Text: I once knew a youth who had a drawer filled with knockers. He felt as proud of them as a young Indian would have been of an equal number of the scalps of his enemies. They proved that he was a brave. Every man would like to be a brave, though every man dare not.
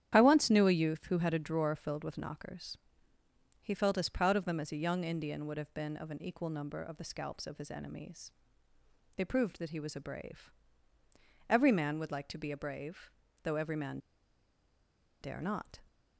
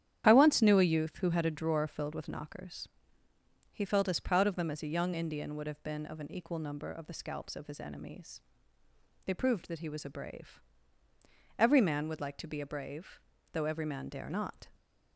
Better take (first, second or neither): second